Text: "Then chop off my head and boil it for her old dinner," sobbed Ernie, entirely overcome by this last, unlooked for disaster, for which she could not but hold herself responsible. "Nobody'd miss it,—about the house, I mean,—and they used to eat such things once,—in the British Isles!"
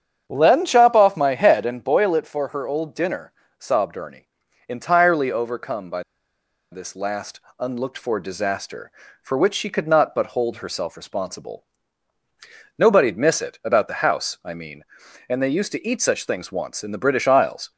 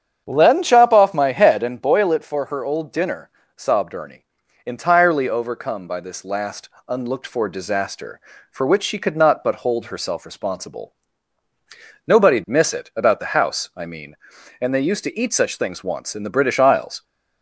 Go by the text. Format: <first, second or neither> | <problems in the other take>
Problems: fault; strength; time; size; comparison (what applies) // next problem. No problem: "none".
second | starts louder than the rest; strong; until 1.2 s; 8 dB; strong in the second // pauses between "by" and "this"; noticeable; at 6.0 s; 0.70 s long